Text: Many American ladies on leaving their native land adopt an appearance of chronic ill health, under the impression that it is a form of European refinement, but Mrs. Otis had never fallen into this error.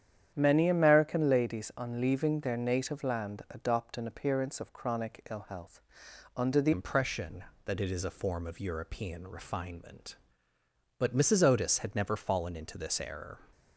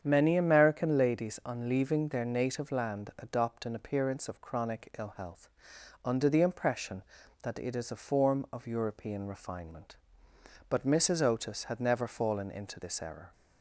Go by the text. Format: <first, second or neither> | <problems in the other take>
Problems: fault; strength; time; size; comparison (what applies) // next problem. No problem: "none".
second | starts louder than the rest; strong; until 1.3 s; 9.5 dB; strong in the second // changes voice at "impression"; from 6.7 s on; 6.6 s long